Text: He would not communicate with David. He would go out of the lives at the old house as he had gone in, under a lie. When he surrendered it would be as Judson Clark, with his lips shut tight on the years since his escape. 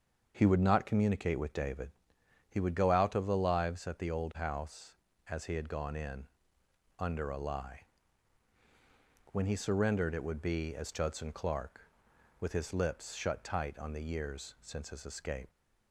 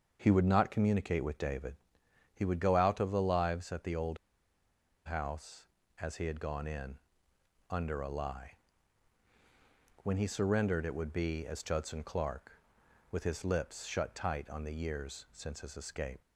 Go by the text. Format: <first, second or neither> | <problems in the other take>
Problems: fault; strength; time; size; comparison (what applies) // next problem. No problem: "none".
first | starts louder than the rest; until 1.2 s; 6.5 dB; also in the first // pauses between "old" and "house"; noticeable; at 4.1 s; 0.89 s long